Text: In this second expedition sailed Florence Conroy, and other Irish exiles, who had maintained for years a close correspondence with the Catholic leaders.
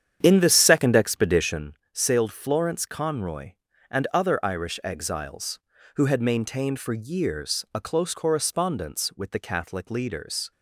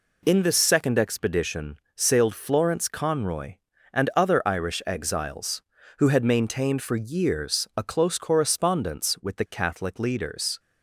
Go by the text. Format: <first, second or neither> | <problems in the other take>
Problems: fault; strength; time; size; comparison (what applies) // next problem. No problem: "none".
second | starts louder than the rest; strong; until 1.7 s; 9 dB // pauses between "expedition" and "sailed"; slight; at 1.7 s; 0.20 s long; slight in the second